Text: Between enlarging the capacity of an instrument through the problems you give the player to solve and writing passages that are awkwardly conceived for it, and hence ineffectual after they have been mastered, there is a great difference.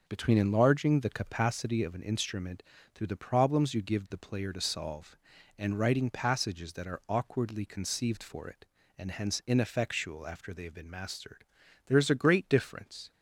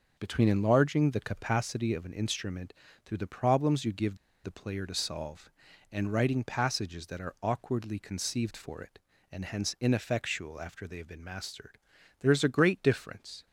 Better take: first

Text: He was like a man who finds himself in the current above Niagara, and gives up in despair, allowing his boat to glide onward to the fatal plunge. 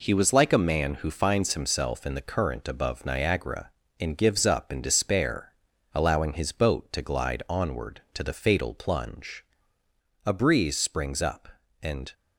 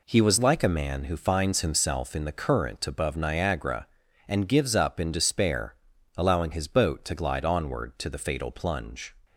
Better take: second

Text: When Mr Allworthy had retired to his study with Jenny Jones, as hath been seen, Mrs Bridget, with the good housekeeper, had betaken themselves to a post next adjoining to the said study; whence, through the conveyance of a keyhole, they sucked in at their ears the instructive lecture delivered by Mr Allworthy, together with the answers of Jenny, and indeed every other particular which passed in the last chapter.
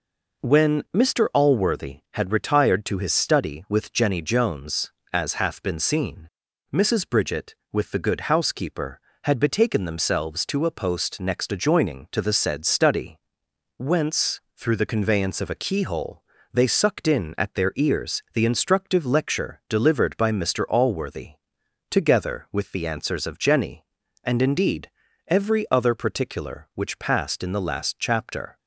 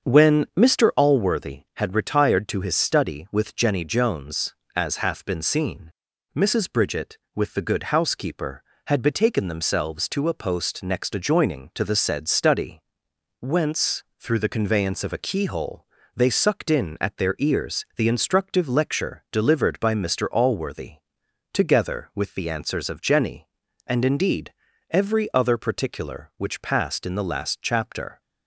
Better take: first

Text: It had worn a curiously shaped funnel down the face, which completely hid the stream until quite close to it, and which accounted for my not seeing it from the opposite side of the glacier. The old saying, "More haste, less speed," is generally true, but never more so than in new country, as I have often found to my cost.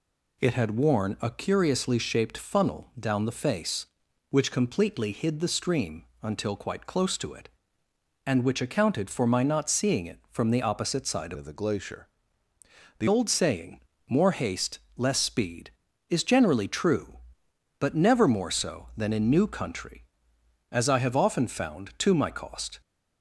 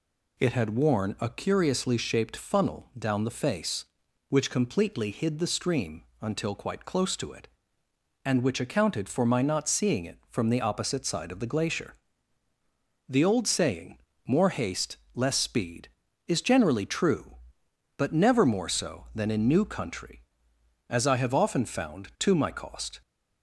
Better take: second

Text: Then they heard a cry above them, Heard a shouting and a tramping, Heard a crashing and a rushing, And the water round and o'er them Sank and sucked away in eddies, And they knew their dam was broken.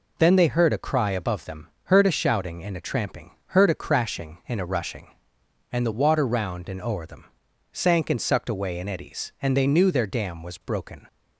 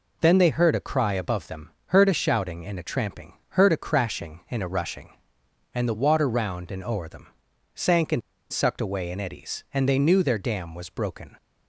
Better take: first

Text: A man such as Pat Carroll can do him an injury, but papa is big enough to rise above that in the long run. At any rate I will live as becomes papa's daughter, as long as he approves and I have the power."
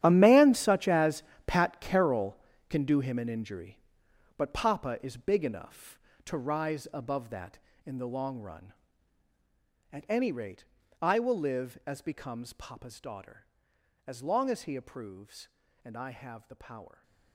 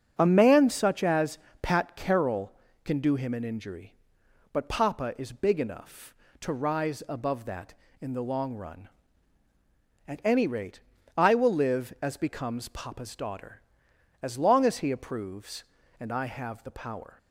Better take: second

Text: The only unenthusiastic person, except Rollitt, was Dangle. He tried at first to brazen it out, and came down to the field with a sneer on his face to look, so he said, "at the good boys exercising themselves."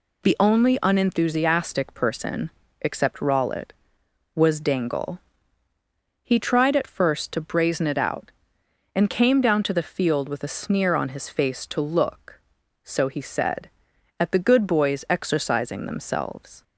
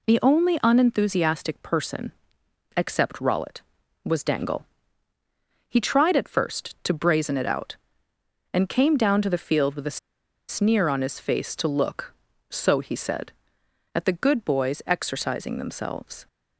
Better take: first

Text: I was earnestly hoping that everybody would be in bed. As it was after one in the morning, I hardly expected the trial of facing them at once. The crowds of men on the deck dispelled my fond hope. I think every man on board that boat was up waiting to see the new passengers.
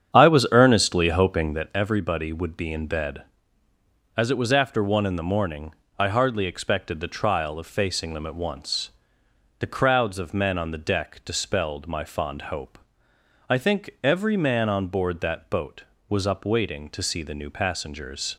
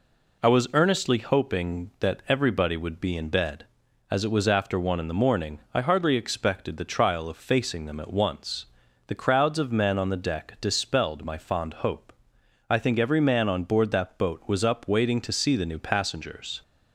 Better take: second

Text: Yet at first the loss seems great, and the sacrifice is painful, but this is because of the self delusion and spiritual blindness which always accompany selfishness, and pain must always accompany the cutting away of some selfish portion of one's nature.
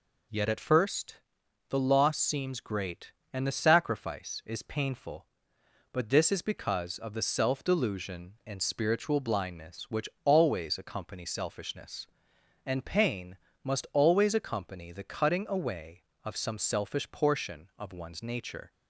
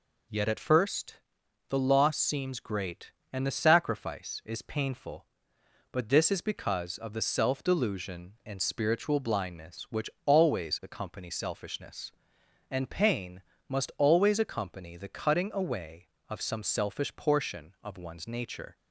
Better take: neither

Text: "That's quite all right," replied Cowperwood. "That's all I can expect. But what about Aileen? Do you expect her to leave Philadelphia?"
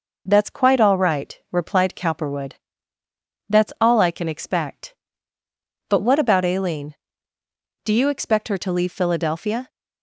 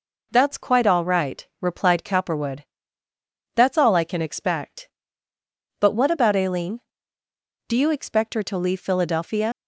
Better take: first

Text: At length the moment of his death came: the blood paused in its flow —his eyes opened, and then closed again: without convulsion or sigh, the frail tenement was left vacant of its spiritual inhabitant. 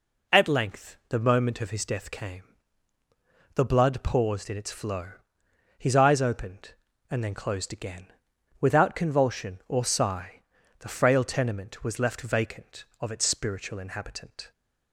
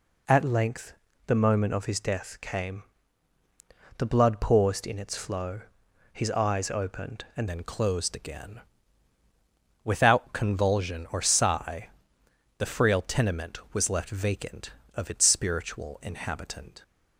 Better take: first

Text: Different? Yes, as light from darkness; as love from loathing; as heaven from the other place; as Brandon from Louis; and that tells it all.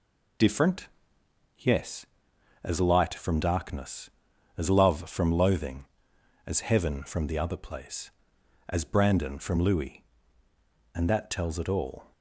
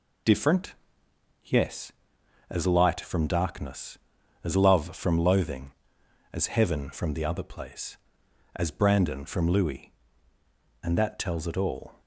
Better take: neither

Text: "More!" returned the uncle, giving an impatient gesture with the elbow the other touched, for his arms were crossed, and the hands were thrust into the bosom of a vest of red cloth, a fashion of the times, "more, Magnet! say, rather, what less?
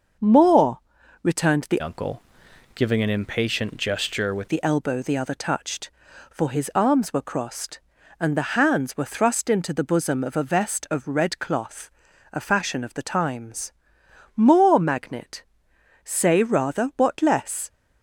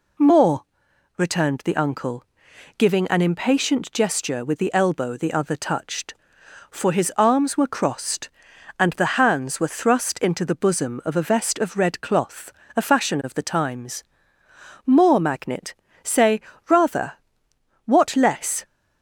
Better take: second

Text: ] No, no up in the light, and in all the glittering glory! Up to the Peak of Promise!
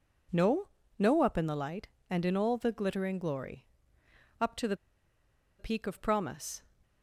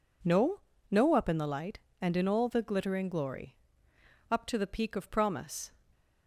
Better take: second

